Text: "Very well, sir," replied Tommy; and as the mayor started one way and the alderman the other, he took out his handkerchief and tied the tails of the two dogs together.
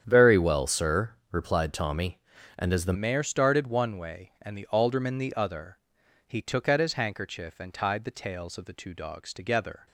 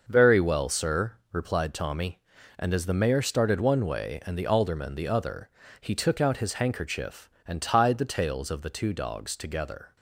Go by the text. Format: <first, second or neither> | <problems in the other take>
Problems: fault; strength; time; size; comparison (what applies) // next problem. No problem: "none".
second | starts louder than the rest; strong; until 1.0 s; 9 dB // changes voice at "mayor"; from 2.9 s on; 6.9 s long